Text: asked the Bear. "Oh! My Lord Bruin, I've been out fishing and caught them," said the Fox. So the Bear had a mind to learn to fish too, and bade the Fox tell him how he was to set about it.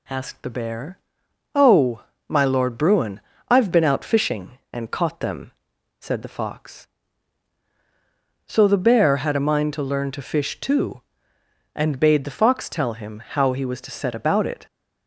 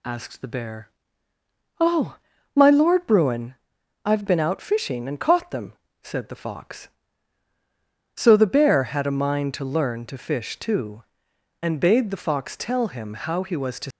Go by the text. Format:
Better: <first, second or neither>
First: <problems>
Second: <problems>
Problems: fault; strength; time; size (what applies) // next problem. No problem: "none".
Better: first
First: none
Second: stops before "set about it"; at 13.9 s